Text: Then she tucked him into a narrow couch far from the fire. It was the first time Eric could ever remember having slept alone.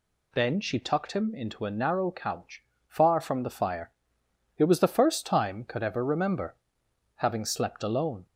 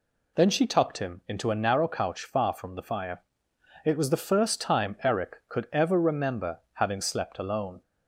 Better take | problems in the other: second | pauses between "couch" and "far"; slight; at 2.6 s; 0.24 s long // skips "Eric"; at 5.6 s // pauses between "remember" and "having"; noticeable; at 6.5 s; 0.60 s long

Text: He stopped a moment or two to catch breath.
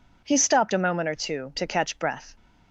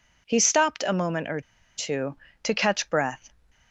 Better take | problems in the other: first | pauses between "or" and "two"; slight; at 1.4 s; 0.35 s long

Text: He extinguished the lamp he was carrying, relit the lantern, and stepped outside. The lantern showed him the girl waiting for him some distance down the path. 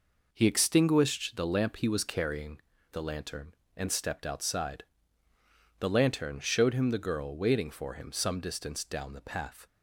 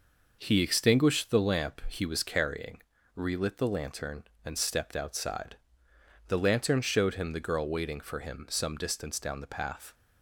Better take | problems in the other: second | skips "relit"; at 2.7 s

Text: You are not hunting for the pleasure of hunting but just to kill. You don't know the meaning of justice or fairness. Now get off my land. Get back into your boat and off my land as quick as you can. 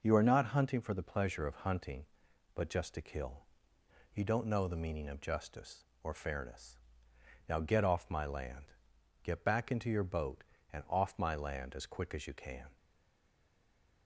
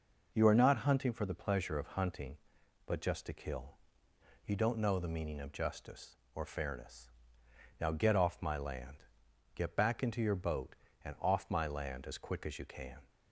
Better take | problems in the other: second | stays silent after the last word; noticeable; from 12.7 s on; 1.3 s long

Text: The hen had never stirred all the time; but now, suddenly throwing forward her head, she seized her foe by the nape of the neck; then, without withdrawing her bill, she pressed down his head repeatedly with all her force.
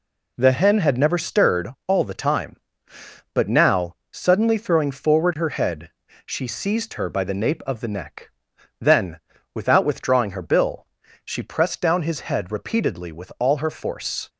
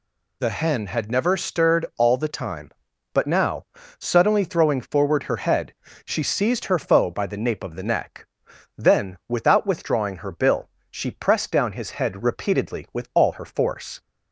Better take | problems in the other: second | pauses between "stirred" and "all"; slight; at 1.6 s; 0.18 s long // skips "foe"; at 7.0 s

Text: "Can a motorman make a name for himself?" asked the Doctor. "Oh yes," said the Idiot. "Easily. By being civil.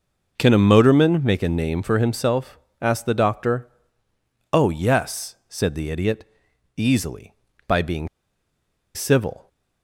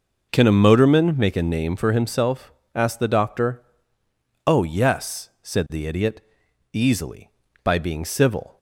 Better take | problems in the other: second | pauses between "being" and "civil"; noticeable; at 8.0 s; 0.87 s long

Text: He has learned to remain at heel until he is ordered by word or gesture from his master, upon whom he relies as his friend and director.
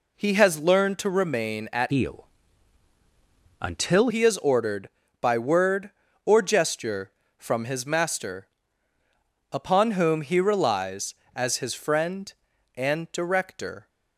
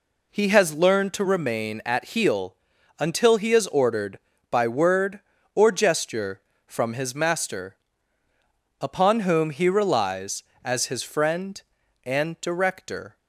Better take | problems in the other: second | changes voice from "heel" to "until"; from 1.9 to 4.0 s; 2.1 s long // pauses between "heel" and "until"; strong; at 2.2 s; 1.3 s long; also in the second

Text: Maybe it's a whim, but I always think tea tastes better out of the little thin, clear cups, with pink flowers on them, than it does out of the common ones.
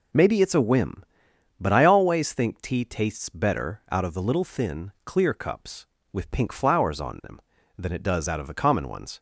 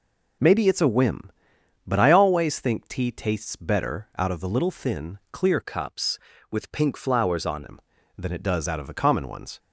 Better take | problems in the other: first | changes voice from "cups" to "on"; from 5.6 to 7.6 s; 2.0 s long

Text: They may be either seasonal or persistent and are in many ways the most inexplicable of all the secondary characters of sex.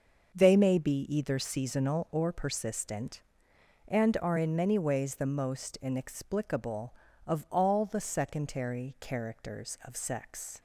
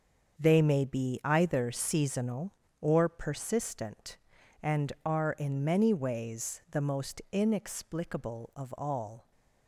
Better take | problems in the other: first | starts louder than the rest; until 1.4 s; 7 dB; also in the first // stops before "the secondary characters of sex"; at 9.3 s

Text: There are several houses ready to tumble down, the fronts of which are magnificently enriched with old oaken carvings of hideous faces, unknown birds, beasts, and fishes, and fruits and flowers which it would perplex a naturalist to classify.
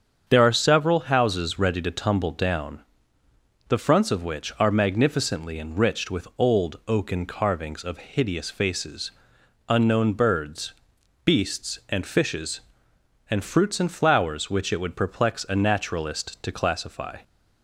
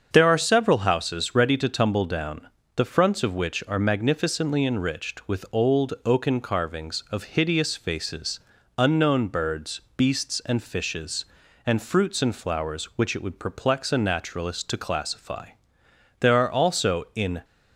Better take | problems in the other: first | starts louder than the rest; until 1.1 s; 7 dB; strong in the first // goes on to say "There are also in"; noticeable; from 16.1 s on; 1.2 s long

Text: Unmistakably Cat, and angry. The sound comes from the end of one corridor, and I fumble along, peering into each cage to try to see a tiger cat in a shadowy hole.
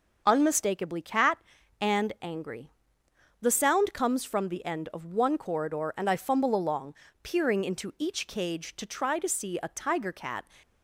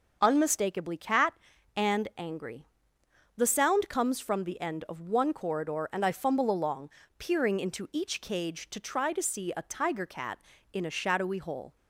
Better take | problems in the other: second | stops before "in a shadowy hole"; at 10.6 s

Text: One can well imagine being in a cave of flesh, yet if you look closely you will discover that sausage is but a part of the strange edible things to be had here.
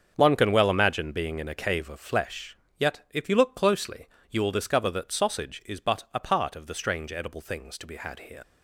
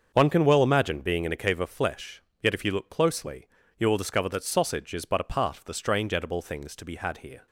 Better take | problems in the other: second | starts louder than the rest; until 1.1 s; 7 dB; also in the second // pauses between "closely" and "you"; slight; at 4.0 s; 0.24 s long; slight in the second // leaves "here" unfinished; at 8.4 s; 45 ms

